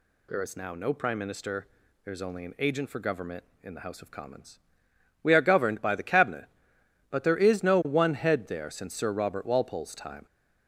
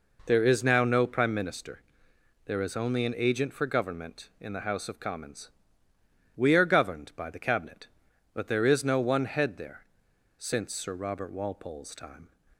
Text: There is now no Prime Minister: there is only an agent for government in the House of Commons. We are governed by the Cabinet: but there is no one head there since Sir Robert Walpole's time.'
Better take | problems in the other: first | pauses between "there" and "since"; noticeable; at 9.8 s; 0.51 s long

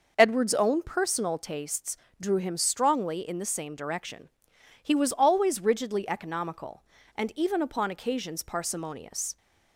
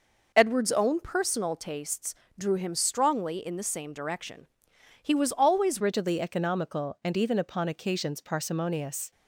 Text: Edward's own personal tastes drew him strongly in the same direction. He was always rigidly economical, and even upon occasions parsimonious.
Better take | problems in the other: first | pauses between "tastes" and "drew"; slight; at 2.1 s; 0.24 s long; slight in the first // changes voice at "rigidly"; from 5.8 s on; 3.3 s long

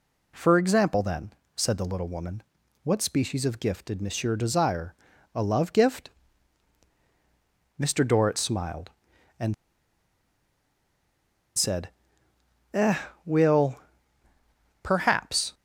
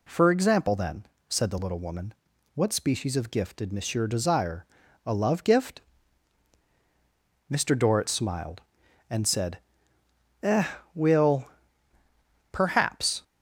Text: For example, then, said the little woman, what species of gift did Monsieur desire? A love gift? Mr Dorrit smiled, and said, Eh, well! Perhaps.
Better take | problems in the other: second | pauses between "and" and "said"; strong; at 9.5 s; 2.0 s long

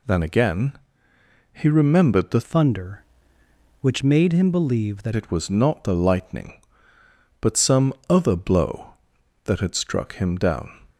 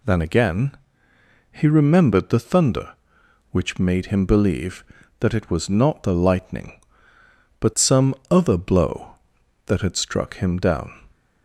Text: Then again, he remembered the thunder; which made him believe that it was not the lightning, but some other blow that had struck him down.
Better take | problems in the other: second | changes voice from "thunder" to "that"; from 2.4 to 5.1 s; 2.7 s long // pauses between "some" and "other"; slight; at 7.9 s; 0.16 s long; slight in the second

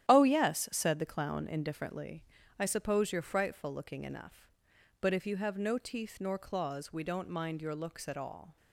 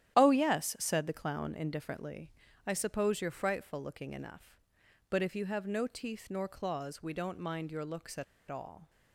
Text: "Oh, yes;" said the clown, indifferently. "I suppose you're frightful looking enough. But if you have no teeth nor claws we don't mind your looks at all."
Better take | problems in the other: first | starts louder than the rest; strong; until 1.2 s; 11.5 dB; strong in the first // pauses between "at" and "all"; slight; at 8.2 s; 0.25 s long

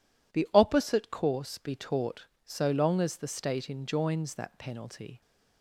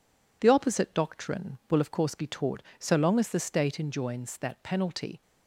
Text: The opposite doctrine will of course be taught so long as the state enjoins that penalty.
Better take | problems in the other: second | skips "doctrine will of"; at 1.1 s

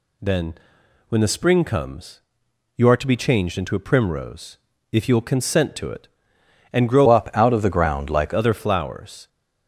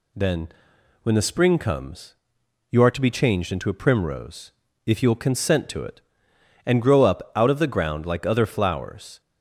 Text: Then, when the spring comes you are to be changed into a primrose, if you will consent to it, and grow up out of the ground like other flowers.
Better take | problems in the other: second | pauses between "comes" and "you"; noticeable; at 2.2 s; 0.58 s long; noticeable in the second // changes voice from "up" to "like"; from 7.0 to 8.3 s; 1.3 s long

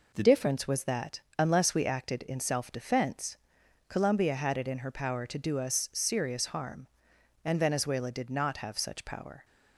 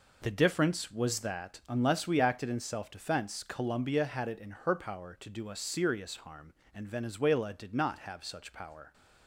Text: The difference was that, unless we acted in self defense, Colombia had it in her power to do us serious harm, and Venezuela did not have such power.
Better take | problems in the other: second | changes voice at "difference"; from 0.2 s on; 9.2 s long

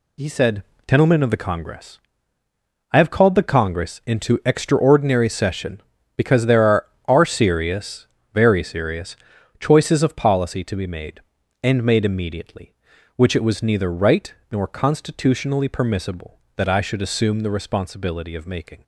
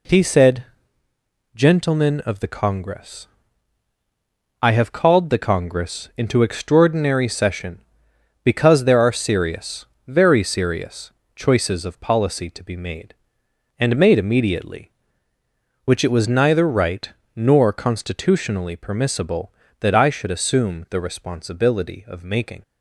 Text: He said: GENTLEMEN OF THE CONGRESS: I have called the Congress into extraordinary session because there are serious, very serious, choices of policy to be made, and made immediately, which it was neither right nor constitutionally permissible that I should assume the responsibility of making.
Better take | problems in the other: second | says "are" twice; at 7.0 s // pauses between "right" and "nor"; slight; at 14.3 s; 0.18 s long; slight in the second

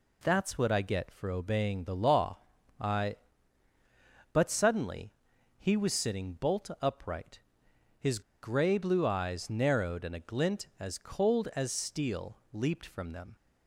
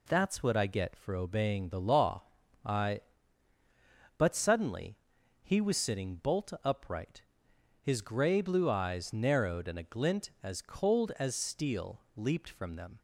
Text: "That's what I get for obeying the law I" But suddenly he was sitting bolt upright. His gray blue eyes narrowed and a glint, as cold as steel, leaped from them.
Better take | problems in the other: second | pauses between "law" and "I"; at 2.3 s; 0.42 s long; also in the second // pauses between "suddenly" and "he"; noticeable; at 5.1 s; 0.48 s long; noticeable in the second // pauses between "His" and "gray"; slight; at 8.2 s; 0.22 s long

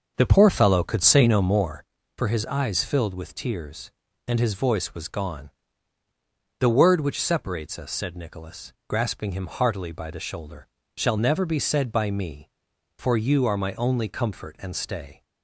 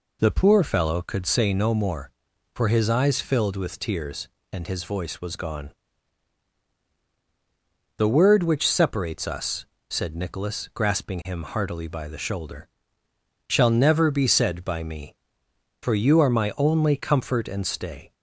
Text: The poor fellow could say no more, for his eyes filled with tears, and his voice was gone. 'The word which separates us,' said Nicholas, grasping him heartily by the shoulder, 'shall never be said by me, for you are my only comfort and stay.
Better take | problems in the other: second | starts louder than the rest; until 1.9 s; 6.5 dB

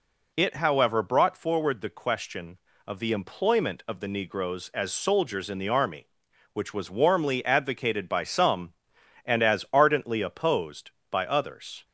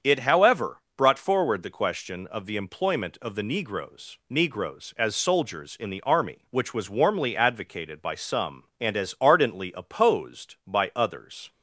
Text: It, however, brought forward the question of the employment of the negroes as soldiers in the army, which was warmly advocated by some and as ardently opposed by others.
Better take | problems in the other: first | starts louder than the rest; strong; until 1.1 s; 7 dB // says "negroes" twice; at 4.2 s

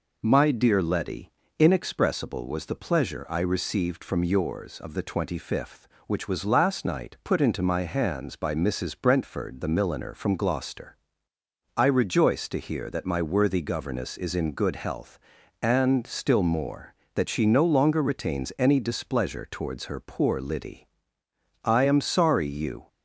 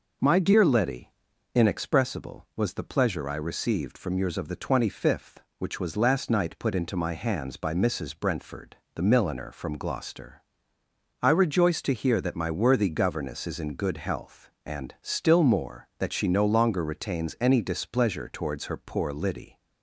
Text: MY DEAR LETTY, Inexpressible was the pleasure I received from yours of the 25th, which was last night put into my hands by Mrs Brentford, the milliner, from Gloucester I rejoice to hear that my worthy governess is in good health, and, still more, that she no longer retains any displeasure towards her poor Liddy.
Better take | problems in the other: second | pauses between "Gloucester" and "I"; noticeable; at 10.9 s; 0.76 s long; noticeable in the second // goes on to say "I am sorry you"; noticeable; from 21.6 s on; 1.2 s long

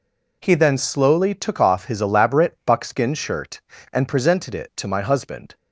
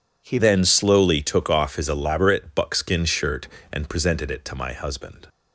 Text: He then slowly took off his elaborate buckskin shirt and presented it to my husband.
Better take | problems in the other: first | changes voice at "then"; from 0.3 s on; 4.9 s long

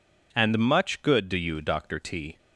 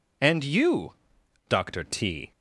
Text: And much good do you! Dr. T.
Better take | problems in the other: first | skips "much good do"; at 0.4 s

